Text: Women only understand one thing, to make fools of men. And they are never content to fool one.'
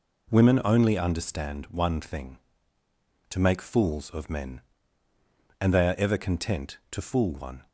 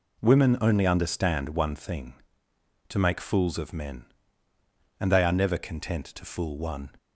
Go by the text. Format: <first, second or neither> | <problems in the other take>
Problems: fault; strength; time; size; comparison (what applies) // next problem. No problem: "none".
second | says "ever" for "never"; at 5.9 s